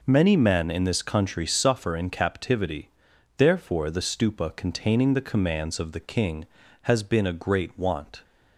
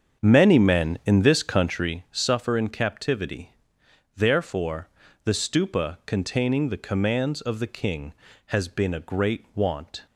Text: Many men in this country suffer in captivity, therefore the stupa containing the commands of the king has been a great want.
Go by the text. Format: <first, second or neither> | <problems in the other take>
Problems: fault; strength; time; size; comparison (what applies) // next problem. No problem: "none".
first | starts louder than the rest; strong; until 1.9 s; 7.5 dB // pauses between "therefore" and "the"; at 4.8 s; 0.38 s long